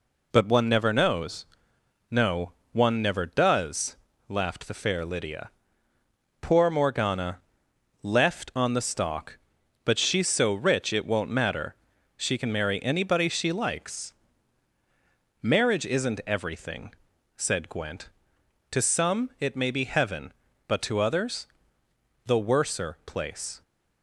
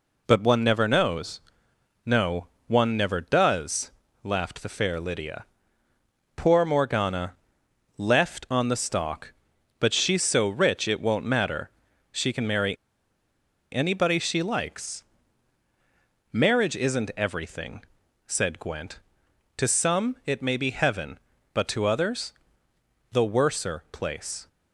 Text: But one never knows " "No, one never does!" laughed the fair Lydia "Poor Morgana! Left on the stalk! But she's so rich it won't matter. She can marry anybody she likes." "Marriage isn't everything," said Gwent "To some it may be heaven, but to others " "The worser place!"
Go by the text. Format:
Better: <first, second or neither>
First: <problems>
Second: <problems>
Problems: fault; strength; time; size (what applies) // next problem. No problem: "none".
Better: first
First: pauses between "Lydia" and "Poor"; noticeable; at 5.4 s; 0.90 s long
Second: pauses between "Lydia" and "Poor"; noticeable; at 5.4 s; 0.90 s long // pauses between "marry" and "anybody"; noticeable; at 12.7 s; 0.95 s long